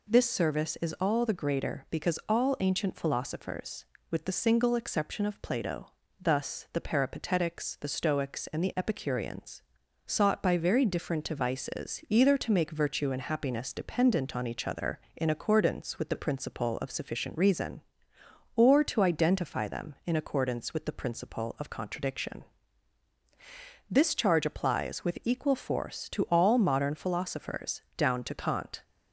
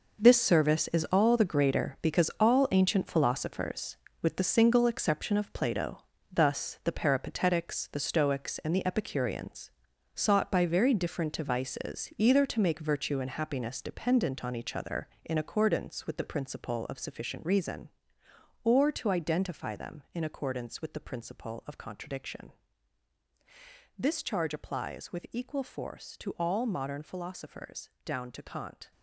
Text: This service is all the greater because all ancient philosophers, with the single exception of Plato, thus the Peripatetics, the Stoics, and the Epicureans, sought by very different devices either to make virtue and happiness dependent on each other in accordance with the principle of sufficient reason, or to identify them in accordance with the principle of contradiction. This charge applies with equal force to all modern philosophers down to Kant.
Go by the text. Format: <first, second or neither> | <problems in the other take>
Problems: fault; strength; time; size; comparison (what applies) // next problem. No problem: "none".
first | gets quieter; strong; throughout; 11 dB